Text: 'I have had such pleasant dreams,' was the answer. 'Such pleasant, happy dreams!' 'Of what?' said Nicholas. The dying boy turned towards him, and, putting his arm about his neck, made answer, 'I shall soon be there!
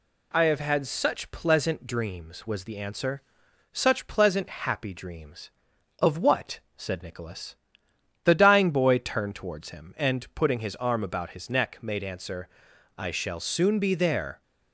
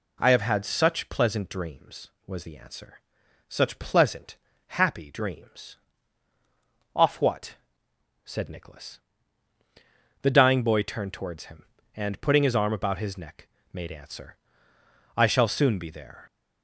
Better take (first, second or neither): first